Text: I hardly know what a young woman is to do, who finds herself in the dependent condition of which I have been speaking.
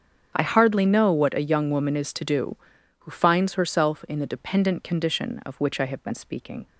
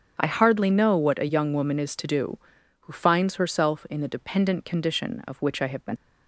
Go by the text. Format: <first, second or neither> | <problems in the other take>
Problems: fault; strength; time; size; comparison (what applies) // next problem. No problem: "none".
first | starts louder than the rest; strong; until 1.1 s; 8 dB; strong in the first // stops before "speaking"; at 5.9 s